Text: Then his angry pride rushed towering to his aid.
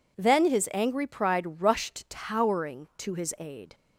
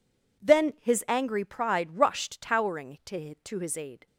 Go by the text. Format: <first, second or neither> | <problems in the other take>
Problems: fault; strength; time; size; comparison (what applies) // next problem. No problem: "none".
first | says "to" twice; at 3.3 s